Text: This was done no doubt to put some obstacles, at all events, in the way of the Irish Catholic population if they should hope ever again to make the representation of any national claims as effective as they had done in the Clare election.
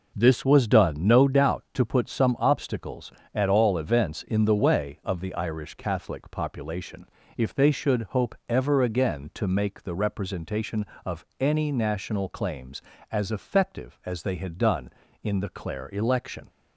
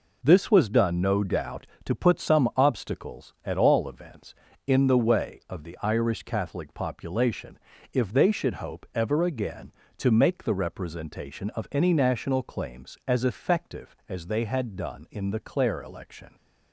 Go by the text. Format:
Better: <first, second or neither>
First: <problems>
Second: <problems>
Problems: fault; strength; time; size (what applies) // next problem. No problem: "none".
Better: neither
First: pauses between "population" and "if"; slight; at 7.0 s; 0.28 s long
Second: pauses between "population" and "if"; slight; at 7.5 s; 0.34 s long